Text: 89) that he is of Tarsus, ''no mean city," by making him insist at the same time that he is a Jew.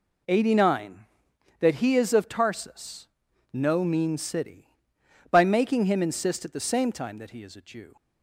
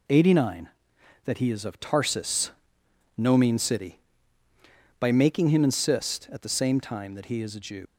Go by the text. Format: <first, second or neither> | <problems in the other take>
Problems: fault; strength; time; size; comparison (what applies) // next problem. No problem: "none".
first | leaves "Jew" unfinished; at 7.8 s; 90 ms